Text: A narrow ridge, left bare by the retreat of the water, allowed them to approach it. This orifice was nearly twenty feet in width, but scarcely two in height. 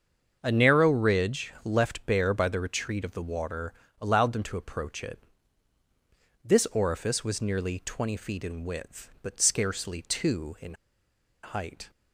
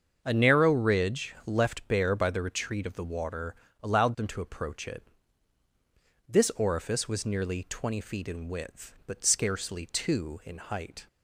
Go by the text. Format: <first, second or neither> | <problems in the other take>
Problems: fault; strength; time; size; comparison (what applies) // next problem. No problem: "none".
second | starts louder than the rest; until 1.4 s; 7 dB; also in the second // pauses between "in" and "height"; noticeable; at 10.7 s; 0.68 s long